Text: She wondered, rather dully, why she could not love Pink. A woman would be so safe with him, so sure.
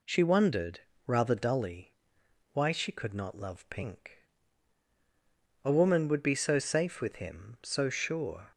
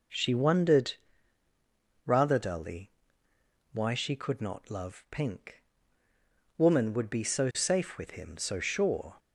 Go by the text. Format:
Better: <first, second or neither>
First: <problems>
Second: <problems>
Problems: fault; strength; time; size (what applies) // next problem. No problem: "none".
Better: first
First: none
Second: skips "A"; at 6.0 s